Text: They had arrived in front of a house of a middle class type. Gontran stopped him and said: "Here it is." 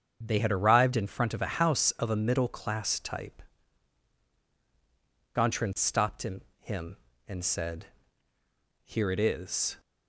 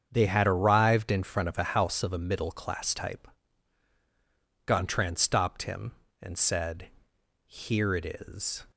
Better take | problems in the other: second | starts louder than the rest; strong; until 1.2 s; 7 dB; strong in the second // says "him" twice; at 6.5 s

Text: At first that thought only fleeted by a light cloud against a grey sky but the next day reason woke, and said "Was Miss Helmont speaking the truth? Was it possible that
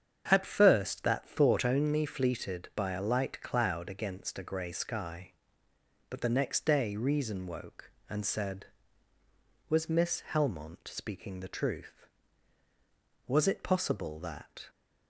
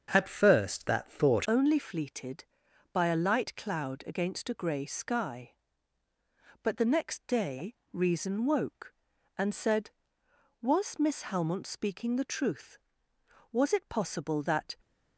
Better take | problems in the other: first | starts louder than the rest; until 1.1 s; 7 dB; strong in the first // changes voice at "only"; from 1.4 s on; 13.3 s long // pauses between "day" and "reason"; slight; at 7.7 s; 0.18 s long

